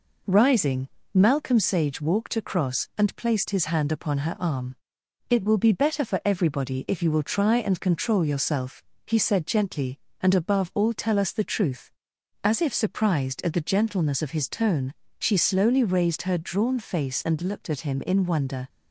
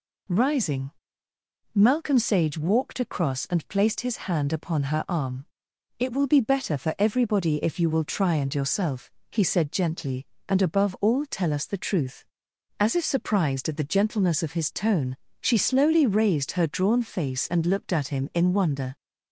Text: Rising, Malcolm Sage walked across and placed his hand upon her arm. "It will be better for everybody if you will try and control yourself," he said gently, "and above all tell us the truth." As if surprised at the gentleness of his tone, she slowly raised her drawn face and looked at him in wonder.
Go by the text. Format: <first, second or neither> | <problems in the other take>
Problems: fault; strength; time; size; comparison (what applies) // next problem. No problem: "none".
first | skips "control"; at 8.5 s